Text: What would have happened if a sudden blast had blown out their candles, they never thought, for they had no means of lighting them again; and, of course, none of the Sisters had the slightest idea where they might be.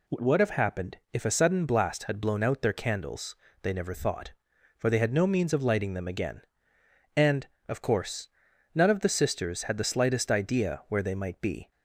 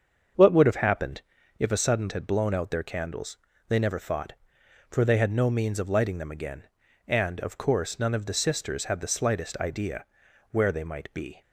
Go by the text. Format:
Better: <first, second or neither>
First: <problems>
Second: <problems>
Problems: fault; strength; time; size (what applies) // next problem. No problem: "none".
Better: first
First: pauses between "happened" and "if"; slight; at 0.9 s; 0.16 s long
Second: starts louder than the rest; strong; until 1.7 s; 7 dB // pauses between "happened" and "if"; at 1.2 s; 0.38 s long // skips "blast"; at 2.1 s // pauses between "idea" and "where"; noticeable; at 10.0 s; 0.46 s long